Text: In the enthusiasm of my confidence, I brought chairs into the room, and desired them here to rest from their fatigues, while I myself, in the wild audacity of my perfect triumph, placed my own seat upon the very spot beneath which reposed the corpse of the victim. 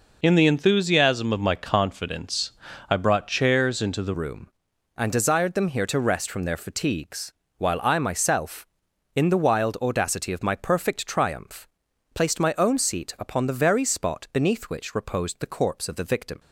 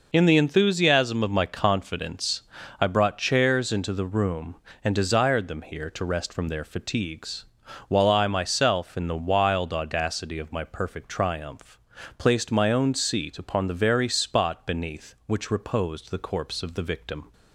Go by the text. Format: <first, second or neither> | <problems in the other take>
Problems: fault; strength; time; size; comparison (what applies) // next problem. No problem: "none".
second | changes voice at "room"; from 4.1 s on; 12.2 s long